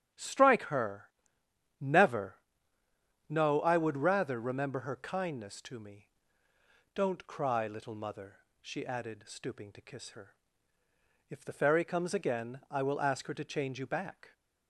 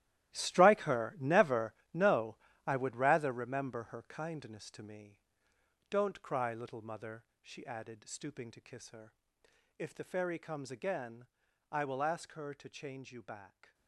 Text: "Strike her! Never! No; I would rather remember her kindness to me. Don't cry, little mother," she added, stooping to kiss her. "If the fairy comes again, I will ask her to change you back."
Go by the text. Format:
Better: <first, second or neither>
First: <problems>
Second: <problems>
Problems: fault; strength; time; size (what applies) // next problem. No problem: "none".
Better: first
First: starts louder than the rest; strong; until 1.8 s; 9 dB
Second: gets quieter; strong; throughout; 15 dB // starts louder than the rest; strong; until 1.4 s; 14.5 dB